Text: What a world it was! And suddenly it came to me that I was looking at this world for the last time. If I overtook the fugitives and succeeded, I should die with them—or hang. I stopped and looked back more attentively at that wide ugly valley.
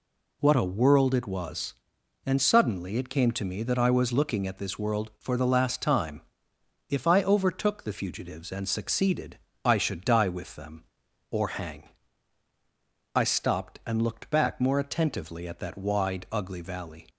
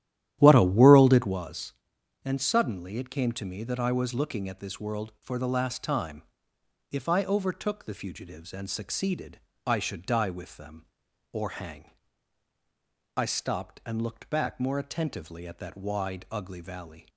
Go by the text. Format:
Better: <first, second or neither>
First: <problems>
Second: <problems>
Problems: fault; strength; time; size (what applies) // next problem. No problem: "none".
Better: first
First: none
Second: starts louder than the rest; strong; until 1.4 s; 12 dB